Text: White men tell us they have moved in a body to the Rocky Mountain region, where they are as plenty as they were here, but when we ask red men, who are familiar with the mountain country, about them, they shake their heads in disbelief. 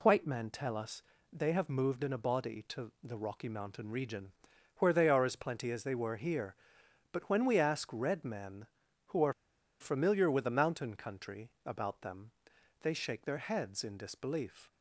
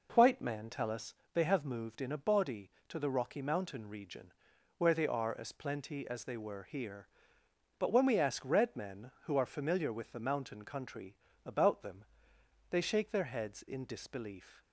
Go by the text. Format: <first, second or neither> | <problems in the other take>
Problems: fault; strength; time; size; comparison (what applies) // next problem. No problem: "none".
second | pauses between "us" and "they"; slight; at 1.0 s; 0.28 s long; slight in the second // pauses between "are" and "familiar"; noticeable; at 9.3 s; 0.47 s long